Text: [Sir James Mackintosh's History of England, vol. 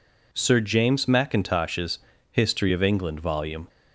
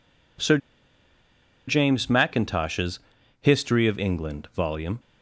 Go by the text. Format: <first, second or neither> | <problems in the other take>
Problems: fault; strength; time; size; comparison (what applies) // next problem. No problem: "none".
first | pauses between "Sir" and "James"; at 0.5 s; 1.1 s long // pauses between "Mackintosh's" and "History"; at 2.9 s; 0.42 s long; slight in the first